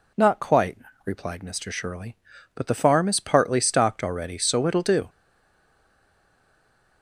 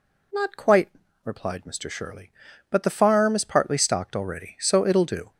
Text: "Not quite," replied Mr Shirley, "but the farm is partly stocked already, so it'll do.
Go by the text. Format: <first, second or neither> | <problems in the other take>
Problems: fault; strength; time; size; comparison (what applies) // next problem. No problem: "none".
second | stays silent after the last word; noticeable; from 5.0 s on; 2.0 s long